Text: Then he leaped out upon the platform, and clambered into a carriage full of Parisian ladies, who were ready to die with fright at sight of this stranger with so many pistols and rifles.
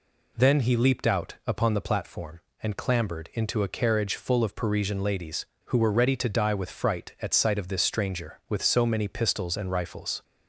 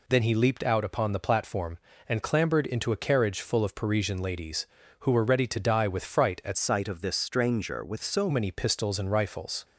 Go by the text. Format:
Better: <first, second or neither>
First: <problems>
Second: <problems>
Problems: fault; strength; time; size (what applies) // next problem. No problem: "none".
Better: first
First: none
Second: changes voice from "sight" to "so"; from 6.5 to 8.2 s; 1.7 s long